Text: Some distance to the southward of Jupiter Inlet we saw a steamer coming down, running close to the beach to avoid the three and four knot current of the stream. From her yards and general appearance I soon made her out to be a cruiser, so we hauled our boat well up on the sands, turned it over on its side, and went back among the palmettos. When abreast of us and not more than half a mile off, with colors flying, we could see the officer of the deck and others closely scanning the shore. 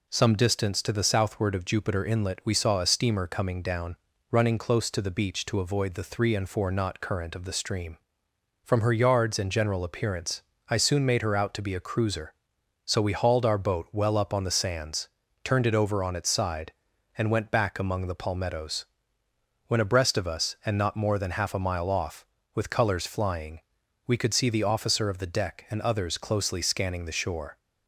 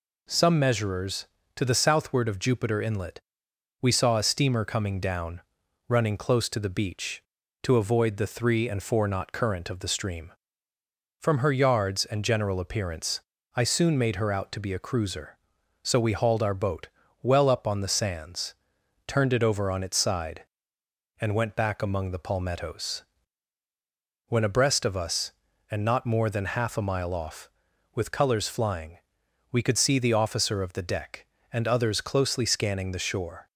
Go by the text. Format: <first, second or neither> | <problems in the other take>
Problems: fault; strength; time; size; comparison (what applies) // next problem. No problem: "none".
first | says "measurers" for "distance"; at 0.5 s // pauses between "Inlet" and "we"; noticeable; at 3.2 s; 0.60 s long // pauses between "appearance" and "I"; slight; at 13.2 s; 0.34 s long; slight in the first // pauses between "boat" and "well"; slight; at 16.8 s; 0.34 s long